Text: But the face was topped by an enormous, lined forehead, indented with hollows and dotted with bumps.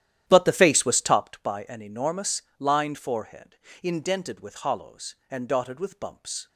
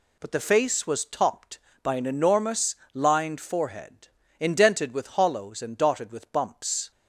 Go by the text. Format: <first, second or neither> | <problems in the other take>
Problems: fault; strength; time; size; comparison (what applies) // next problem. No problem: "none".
second | starts louder than the rest; strong; until 1.3 s; 11.5 dB